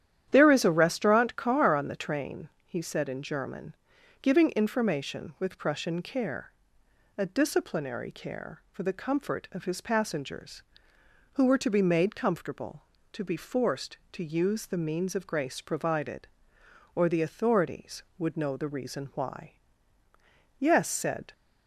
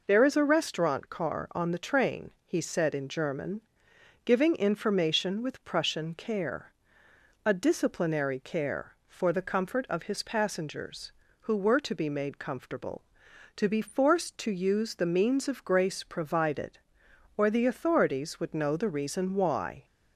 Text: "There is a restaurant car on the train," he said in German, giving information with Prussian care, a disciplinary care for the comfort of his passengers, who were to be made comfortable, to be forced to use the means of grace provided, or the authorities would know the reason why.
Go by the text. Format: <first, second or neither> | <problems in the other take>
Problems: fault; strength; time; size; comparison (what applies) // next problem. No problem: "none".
second | starts louder than the rest; strong; until 1.3 s; 11 dB // goes on to say "Yes said"; noticeable; from 20.5 s on; 0.74 s long